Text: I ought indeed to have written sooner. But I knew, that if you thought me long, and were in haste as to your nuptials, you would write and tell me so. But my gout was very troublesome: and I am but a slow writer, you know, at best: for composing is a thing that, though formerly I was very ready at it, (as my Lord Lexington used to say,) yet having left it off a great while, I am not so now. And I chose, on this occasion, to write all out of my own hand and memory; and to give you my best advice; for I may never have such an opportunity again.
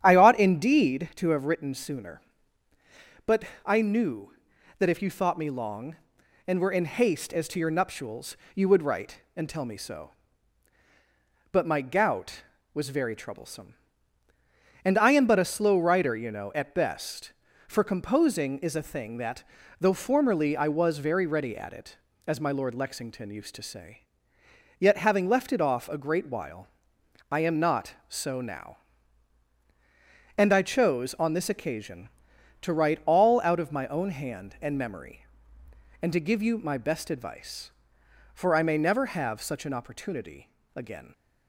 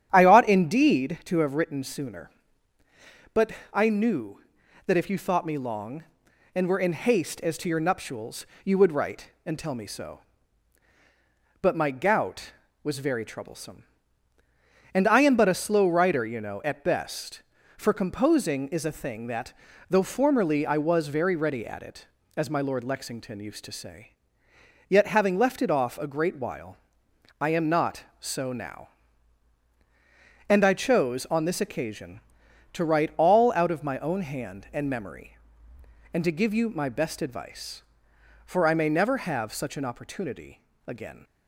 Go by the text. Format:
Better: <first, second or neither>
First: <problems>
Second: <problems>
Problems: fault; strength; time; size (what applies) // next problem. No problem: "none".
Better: neither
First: starts louder than the rest; strong; until 1.0 s; 10 dB // pauses between "But" and "I"; slight; at 3.4 s; 0.22 s long // pauses between "opportunity" and "again"; slight; at 40.4 s; 0.26 s long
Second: starts louder than the rest; strong; until 1.1 s; 9.5 dB // pauses between "But" and "I"; slight; at 3.5 s; 0.22 s long // pauses between "opportunity" and "again"; slight; at 40.5 s; 0.26 s long